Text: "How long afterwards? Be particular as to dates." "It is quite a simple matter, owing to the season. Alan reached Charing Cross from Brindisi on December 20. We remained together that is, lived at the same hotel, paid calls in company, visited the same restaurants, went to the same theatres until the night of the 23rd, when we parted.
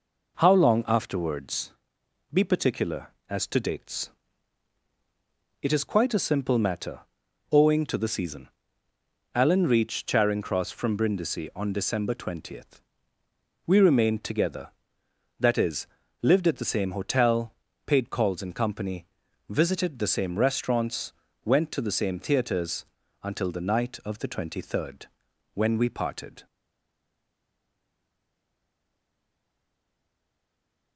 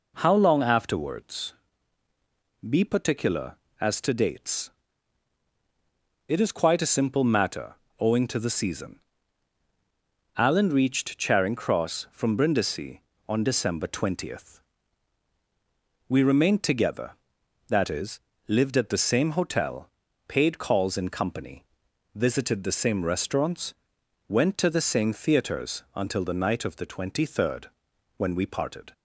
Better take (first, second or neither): second